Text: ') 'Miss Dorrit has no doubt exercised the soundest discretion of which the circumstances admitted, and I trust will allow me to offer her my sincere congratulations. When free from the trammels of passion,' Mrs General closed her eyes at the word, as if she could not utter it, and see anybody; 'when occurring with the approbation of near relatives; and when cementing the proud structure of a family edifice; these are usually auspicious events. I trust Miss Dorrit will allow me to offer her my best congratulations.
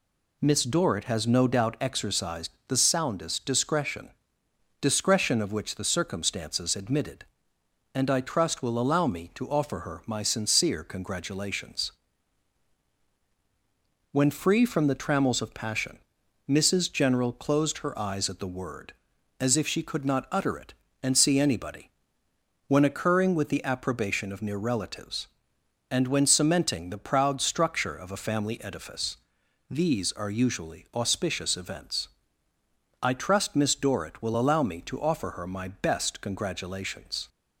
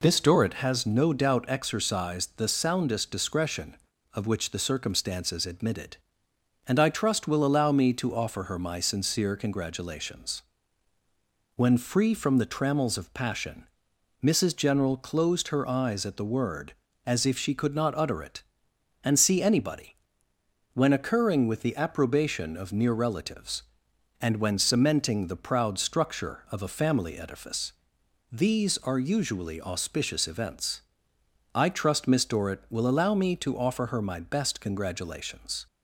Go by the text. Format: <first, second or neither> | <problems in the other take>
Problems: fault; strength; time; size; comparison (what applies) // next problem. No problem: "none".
second | pauses between "exercised" and "the"; slight; at 2.5 s; 0.18 s long // says "discretion" twice; at 4.8 s